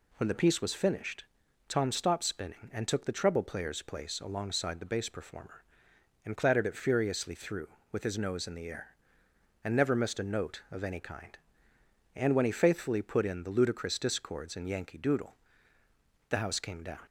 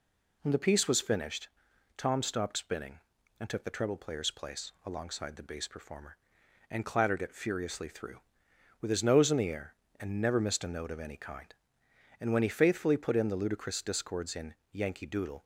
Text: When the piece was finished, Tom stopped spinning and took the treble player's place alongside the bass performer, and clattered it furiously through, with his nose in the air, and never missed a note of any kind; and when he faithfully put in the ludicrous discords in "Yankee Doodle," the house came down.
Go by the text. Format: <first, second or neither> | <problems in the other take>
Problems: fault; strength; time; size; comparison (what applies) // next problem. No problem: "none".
first | pauses between "in" and "Yankee"; slight; at 14.5 s; 0.18 s long // stops before "the house came down"; at 15.4 s